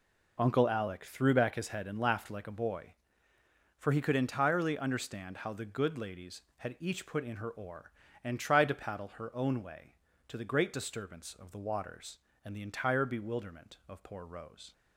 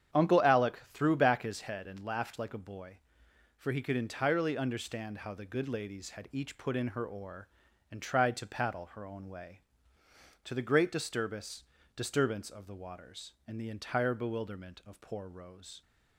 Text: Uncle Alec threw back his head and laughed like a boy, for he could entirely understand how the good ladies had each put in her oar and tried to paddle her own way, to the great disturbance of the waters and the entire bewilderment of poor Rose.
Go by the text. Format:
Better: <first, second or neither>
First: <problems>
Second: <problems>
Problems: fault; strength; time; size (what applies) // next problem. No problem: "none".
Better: first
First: none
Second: starts louder than the rest; strong; until 1.2 s; 9 dB // says "disturbance" twice; at 11.9 s